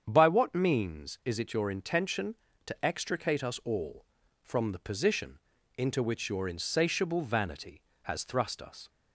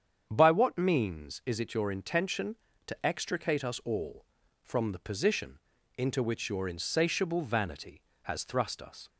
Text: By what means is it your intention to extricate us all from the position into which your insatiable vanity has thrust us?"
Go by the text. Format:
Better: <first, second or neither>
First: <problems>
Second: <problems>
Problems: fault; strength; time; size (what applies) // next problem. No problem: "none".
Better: neither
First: starts louder than the rest; strong; until 1.0 s; 8 dB // pauses between "position" and "into"; at 5.3 s; 0.38 s long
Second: starts louder than the rest; strong; until 1.3 s; 8 dB // pauses between "position" and "into"; at 5.5 s; 0.38 s long